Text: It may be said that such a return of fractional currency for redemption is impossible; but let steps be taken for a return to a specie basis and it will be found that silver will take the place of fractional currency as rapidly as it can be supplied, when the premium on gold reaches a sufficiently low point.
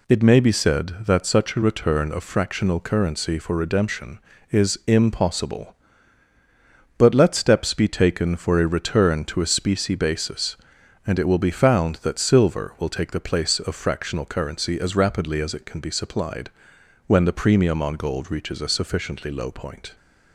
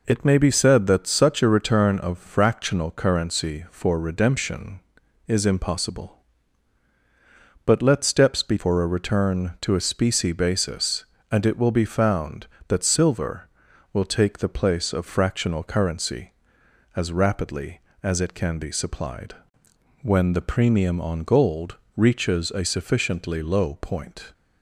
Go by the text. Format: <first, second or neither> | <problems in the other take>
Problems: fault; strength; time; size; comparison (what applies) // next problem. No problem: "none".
first | skips "taken"; at 8.5 s // pauses between "gold" and "reaches"; slight; at 21.7 s; 0.18 s long